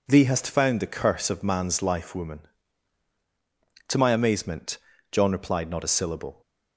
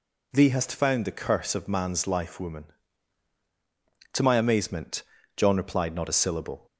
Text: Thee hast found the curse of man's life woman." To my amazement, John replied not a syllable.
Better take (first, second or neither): second